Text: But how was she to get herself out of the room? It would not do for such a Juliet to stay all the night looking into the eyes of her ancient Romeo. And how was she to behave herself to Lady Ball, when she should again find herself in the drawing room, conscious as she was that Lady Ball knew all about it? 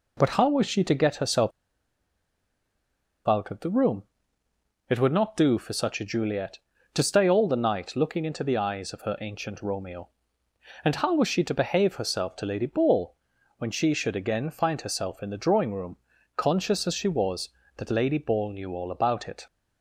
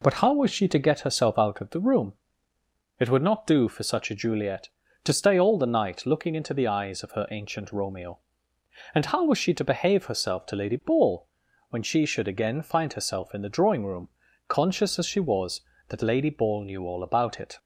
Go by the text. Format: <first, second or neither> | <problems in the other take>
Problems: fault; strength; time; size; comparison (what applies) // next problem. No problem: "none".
second | pauses between "herself" and "out"; strong; at 1.5 s; 1.7 s long